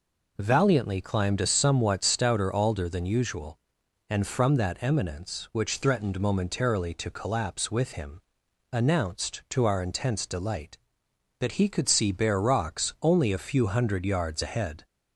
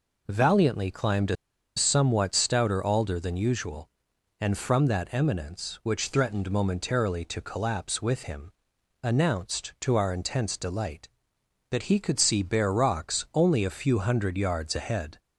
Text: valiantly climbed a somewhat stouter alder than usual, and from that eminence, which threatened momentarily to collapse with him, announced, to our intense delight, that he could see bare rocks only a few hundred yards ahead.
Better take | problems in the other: first | pauses between "a" and "somewhat"; at 1.3 s; 0.41 s long

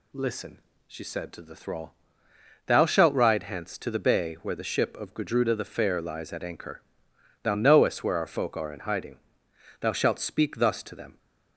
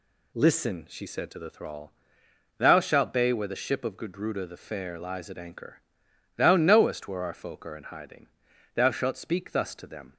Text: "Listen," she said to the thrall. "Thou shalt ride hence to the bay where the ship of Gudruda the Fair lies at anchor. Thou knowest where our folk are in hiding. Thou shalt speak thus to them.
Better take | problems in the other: first | skips "ride hence to the"; at 3.1 s

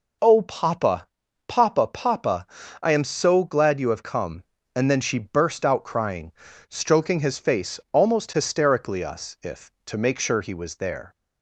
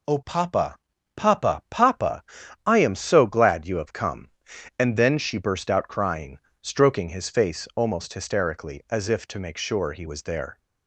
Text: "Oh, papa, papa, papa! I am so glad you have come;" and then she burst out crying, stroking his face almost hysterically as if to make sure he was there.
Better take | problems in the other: second | says "us" for "as"; at 9.0 s

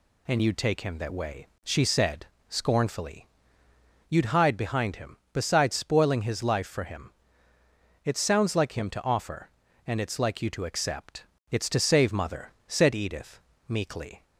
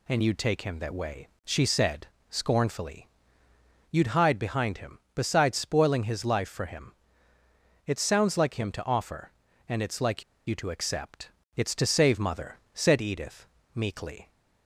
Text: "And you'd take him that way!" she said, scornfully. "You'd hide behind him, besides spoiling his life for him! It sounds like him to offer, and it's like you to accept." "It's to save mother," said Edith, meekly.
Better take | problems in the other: first | pauses between "like" and "you"; slight; at 10.2 s; 0.25 s long

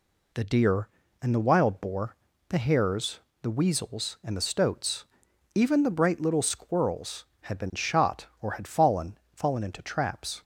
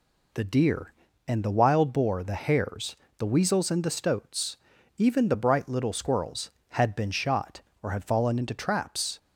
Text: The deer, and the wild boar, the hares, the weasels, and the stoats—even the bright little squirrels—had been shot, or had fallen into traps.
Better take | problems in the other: second | says "fallen" twice; at 9.3 s

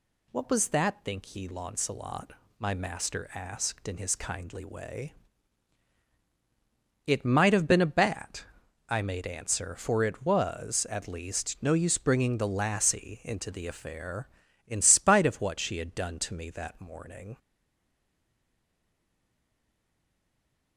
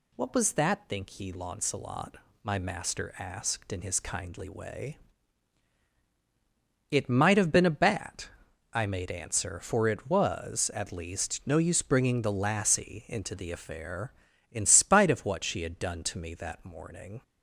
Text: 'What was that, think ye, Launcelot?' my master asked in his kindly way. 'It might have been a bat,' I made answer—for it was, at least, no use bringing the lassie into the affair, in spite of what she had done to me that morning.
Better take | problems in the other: second | stays silent after the last word; strong; from 17.3 s on; 3.4 s long

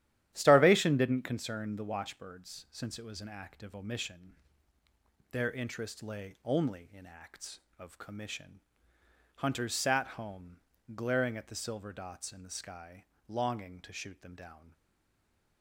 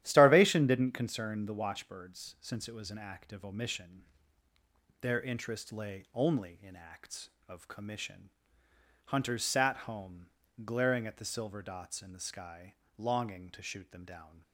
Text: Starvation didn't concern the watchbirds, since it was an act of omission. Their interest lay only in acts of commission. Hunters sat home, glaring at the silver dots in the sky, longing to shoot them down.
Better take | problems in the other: second | starts louder than the rest; strong; until 1.3 s; 12 dB; strong in the second // stays silent after the last word; slight; from 14.7 s on; 0.9 s long

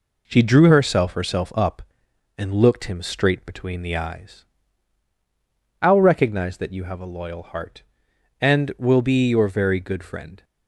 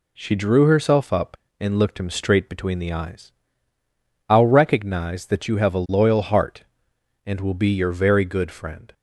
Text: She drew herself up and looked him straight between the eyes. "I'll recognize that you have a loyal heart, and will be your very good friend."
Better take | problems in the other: second | says "herself" twice; at 1.1 s

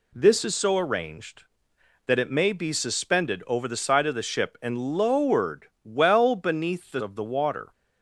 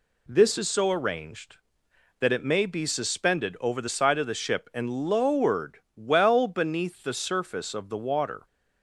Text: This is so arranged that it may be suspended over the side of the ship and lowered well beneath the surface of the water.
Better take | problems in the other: second | pauses between "lowered" and "well"; slight; at 5.6 s; 0.18 s long; slight in the second // skips "surface"; at 7.0 s

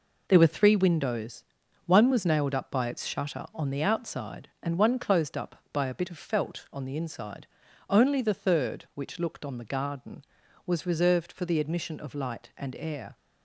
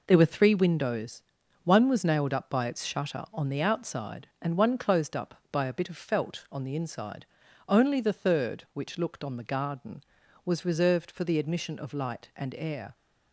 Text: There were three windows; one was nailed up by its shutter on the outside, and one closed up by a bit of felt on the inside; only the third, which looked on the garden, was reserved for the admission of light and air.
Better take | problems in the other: neither | none

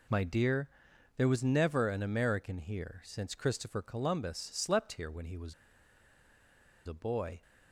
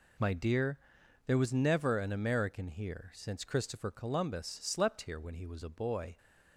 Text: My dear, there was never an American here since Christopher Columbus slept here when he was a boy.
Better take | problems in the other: second | pauses between "was" and "a"; strong; at 5.5 s; 1.3 s long

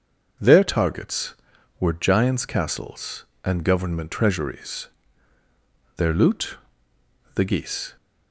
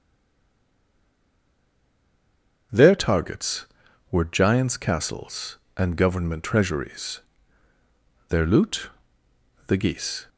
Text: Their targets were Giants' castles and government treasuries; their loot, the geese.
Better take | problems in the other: first | stays silent before the first word; strong; until 2.7 s; 2.7 s long // starts louder than the rest; until 4.1 s; 6.5 dB; also in the first

